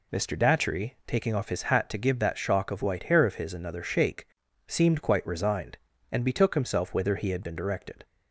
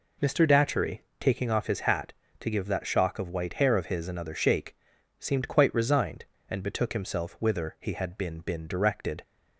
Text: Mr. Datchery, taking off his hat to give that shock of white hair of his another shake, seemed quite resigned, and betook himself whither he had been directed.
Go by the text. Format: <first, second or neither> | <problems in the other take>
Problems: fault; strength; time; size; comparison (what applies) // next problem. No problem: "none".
first | says "been" twice; at 8.4 s